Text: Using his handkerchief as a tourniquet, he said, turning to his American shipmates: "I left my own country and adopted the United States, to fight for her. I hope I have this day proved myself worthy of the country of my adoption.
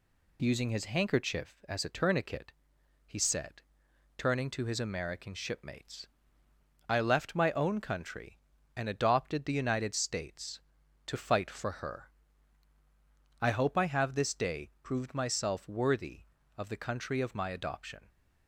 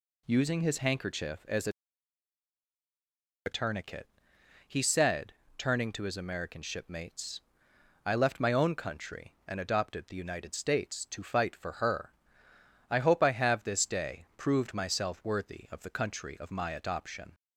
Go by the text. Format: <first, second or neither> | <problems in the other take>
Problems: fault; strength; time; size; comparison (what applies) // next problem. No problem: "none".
first | says "a" twice; at 3.4 s